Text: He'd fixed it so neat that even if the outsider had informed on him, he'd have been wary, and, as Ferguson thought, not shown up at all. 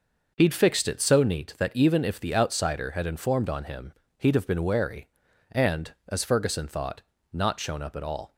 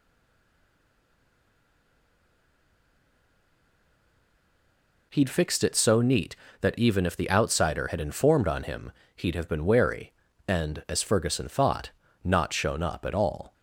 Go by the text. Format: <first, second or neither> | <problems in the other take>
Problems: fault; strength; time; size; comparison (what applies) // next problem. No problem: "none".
first | stays silent before the first word; strong; until 5.1 s; 5.1 s long